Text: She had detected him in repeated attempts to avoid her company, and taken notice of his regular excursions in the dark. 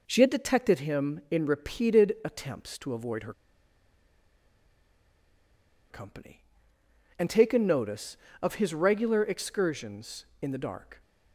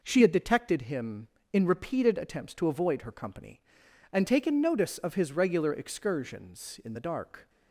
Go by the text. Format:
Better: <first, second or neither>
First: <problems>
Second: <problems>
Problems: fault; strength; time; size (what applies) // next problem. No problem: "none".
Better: second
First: pauses between "her" and "company"; strong; at 3.3 s; 2.5 s long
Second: none